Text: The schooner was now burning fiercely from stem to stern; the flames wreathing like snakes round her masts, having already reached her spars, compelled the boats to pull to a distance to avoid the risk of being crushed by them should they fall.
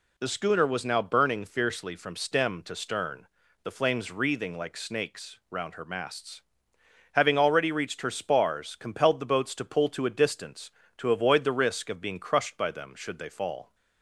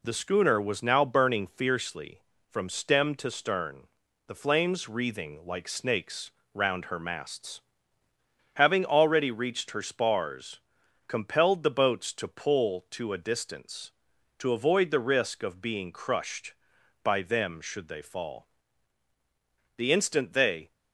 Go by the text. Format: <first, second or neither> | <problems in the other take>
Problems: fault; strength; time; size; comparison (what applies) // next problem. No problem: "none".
first | pauses between "snakes" and "round"; slight; at 6.3 s; 0.22 s long // goes on to say "The instant they"; noticeable; from 19.7 s on; 0.96 s long